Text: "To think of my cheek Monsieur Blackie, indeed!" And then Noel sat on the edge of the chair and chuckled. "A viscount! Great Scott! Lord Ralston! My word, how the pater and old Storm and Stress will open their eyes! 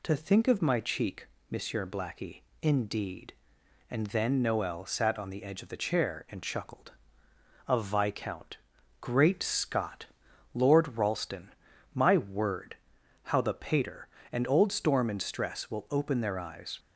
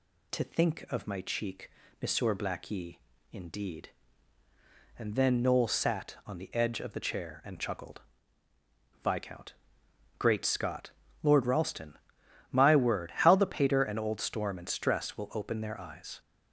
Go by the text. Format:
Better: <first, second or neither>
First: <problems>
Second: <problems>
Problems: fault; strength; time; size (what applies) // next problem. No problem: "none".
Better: first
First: pauses between "cheek" and "Monsieur"; slight; at 1.2 s; 0.24 s long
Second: pauses between "cheek" and "Monsieur"; slight; at 1.7 s; 0.28 s long // skips "A"; at 8.5 s